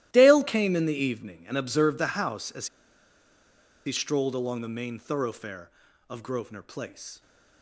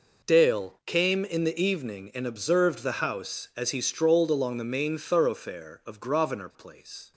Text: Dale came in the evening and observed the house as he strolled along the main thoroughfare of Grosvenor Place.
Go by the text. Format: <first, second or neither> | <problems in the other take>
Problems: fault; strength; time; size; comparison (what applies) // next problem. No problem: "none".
second | starts louder than the rest; strong; until 1.1 s; 14.5 dB // pauses between "as" and "he"; at 2.6 s; 1.1 s long